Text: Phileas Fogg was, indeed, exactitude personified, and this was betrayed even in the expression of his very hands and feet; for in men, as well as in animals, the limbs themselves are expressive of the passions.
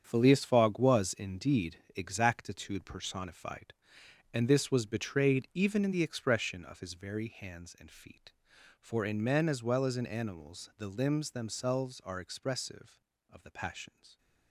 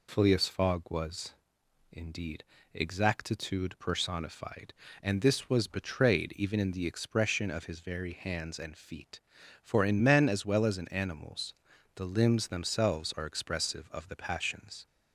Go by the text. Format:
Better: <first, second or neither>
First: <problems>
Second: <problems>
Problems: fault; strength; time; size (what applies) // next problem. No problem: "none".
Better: second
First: gets quieter; strong; throughout; 10 dB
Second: none